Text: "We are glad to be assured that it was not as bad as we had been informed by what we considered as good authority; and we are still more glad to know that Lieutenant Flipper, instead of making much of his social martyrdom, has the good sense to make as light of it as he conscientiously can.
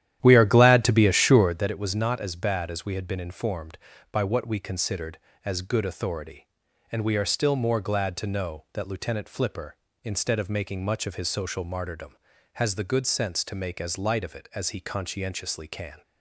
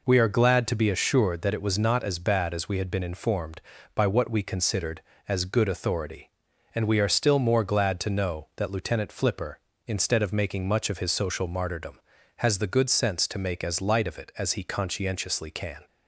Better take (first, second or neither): second